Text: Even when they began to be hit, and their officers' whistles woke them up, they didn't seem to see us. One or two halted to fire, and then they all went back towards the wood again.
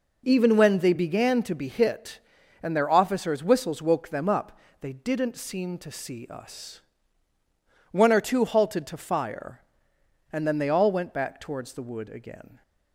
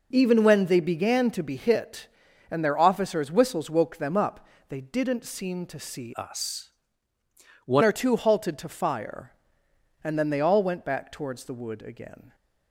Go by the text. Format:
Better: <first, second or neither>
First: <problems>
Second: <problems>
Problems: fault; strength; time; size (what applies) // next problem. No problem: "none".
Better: first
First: none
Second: changes voice from "us" to "One"; from 6.1 to 7.8 s; 1.7 s long